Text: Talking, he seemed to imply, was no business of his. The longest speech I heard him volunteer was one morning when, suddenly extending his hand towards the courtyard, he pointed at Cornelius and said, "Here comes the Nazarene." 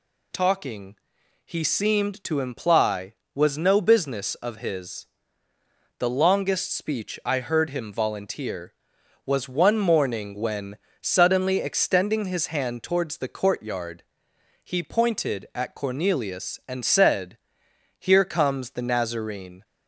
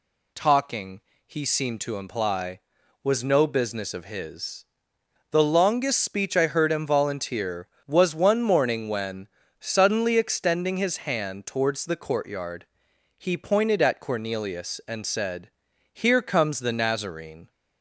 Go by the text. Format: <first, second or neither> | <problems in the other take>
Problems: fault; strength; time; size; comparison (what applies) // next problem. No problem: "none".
neither | none